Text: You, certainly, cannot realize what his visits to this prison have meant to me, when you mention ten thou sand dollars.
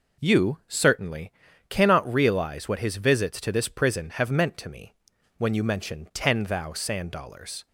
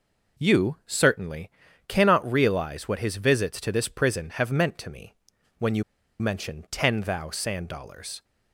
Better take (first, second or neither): first